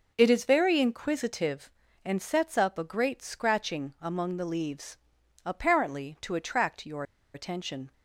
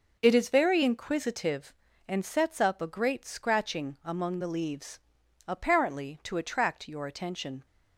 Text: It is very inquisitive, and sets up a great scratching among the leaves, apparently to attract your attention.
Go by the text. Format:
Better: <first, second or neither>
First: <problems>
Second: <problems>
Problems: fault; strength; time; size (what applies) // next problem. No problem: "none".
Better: second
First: pauses between "your" and "attention"; slight; at 7.0 s; 0.31 s long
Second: none